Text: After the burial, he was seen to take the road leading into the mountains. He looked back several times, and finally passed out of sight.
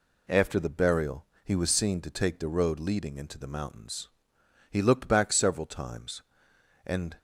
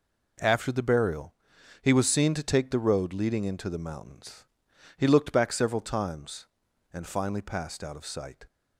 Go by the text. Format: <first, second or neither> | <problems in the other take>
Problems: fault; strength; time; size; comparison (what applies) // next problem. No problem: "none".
second | stops before "finally passed out of sight"; at 7.1 s